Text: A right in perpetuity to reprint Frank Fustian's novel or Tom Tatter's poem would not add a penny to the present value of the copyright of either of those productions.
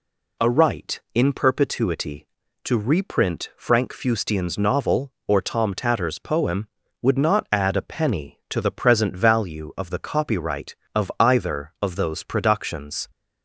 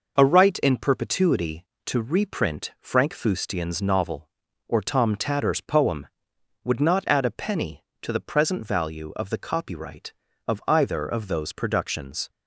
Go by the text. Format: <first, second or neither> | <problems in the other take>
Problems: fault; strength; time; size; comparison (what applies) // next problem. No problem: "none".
neither | none